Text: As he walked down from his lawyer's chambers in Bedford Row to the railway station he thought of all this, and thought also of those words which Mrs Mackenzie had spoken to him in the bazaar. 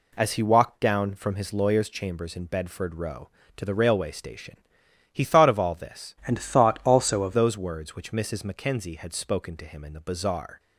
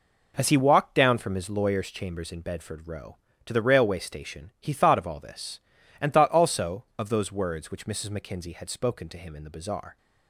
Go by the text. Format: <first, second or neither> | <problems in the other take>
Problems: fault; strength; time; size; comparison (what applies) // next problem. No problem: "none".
second | pauses between "station" and "he"; noticeable; at 4.5 s; 0.58 s long // changes voice from "and" to "of"; from 6.2 to 7.3 s; 1.1 s long